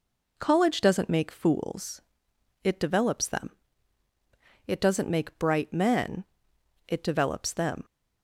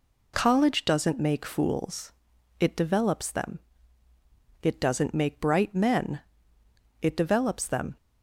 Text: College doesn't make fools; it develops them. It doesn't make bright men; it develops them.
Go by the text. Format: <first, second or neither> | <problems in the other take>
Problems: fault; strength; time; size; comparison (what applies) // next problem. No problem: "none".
neither | none